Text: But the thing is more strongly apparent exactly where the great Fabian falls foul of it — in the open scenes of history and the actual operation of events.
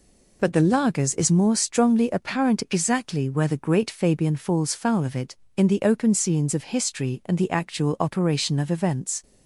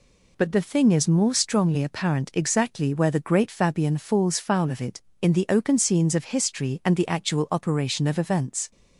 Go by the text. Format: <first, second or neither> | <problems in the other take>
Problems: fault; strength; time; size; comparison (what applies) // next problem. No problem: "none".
second | says "lagers" for "thing"; at 0.6 s